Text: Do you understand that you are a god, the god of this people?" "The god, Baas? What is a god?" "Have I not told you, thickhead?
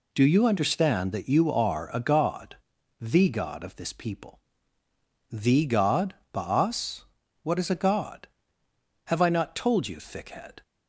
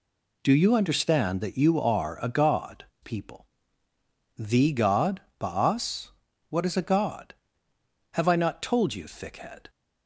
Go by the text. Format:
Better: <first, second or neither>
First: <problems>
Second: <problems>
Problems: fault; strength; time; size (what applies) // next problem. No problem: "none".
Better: first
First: none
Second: skips "the god of this"; at 2.9 s